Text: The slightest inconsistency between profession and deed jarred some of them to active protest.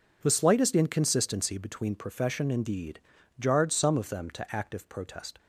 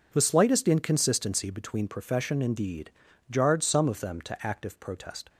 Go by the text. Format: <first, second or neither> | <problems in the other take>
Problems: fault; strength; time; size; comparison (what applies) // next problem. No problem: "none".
neither | pauses between "deed" and "jarred"; the same in both